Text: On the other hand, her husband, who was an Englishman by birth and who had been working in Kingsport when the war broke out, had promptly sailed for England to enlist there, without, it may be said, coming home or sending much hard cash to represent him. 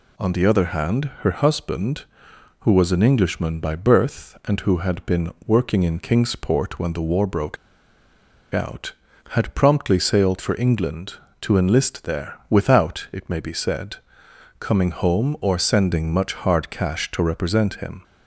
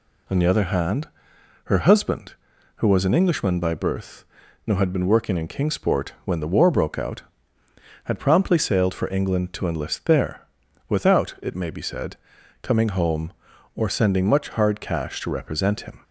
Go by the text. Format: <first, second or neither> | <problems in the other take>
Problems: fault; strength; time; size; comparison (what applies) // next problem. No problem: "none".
second | pauses between "broke" and "out"; noticeable; at 7.5 s; 0.96 s long